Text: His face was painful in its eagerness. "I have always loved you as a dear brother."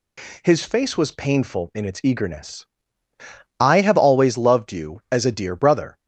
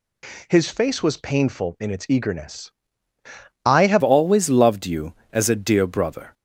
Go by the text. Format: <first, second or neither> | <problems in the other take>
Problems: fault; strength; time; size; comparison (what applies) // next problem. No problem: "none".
first | changes voice at "always"; from 4.0 s on; 2.3 s long